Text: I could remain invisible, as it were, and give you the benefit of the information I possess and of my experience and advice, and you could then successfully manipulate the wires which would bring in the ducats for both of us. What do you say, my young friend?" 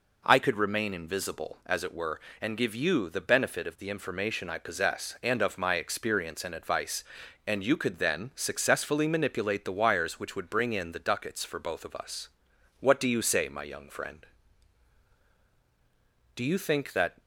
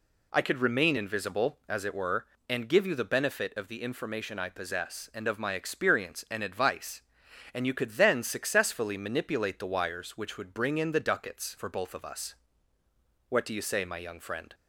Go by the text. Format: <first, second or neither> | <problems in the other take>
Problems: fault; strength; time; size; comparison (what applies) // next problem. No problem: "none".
second | goes on to say "Do you think that"; noticeable; from 16.3 s on; 0.84 s long